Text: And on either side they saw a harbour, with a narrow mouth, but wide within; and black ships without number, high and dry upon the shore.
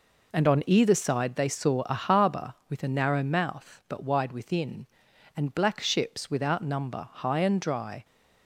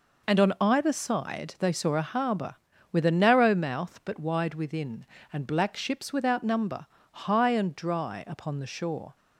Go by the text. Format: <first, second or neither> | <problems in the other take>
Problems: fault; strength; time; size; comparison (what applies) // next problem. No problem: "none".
second | stops before "upon the shore"; at 8.0 s